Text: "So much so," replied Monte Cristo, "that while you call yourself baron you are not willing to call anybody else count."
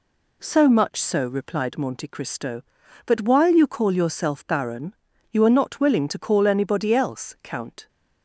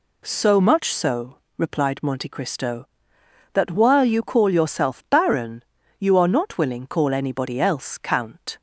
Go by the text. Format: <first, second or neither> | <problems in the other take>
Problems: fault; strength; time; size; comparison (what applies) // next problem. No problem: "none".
first | pauses between "baron" and "you"; slight; at 5.6 s; 0.36 s long; slight in the first // skips "to"; at 6.8 s